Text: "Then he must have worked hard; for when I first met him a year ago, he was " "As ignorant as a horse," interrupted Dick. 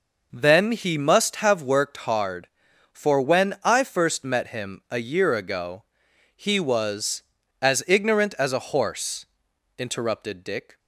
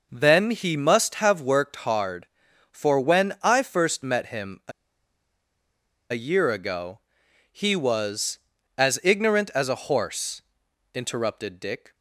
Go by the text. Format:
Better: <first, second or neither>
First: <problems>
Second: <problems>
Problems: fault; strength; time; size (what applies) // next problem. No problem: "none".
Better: first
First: none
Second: pauses between "a" and "year"; strong; at 4.7 s; 1.4 s long